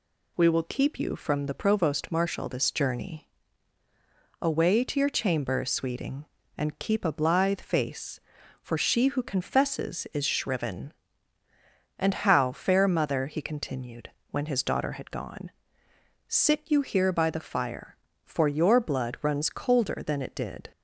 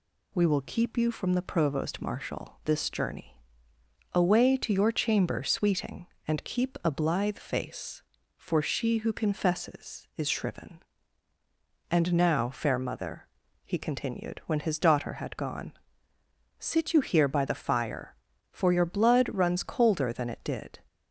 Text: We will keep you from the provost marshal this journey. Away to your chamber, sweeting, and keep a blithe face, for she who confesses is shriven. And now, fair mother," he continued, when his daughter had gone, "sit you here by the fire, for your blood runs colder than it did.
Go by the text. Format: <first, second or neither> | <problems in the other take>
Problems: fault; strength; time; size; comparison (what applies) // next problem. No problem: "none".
second | says "how" for "now"; at 12.1 s